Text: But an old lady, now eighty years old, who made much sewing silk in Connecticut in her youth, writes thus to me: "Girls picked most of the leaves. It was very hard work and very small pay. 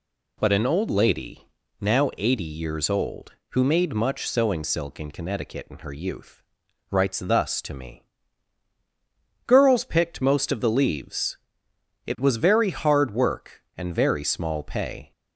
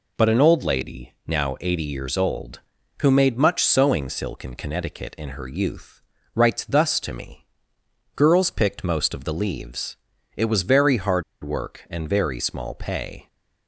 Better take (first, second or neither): first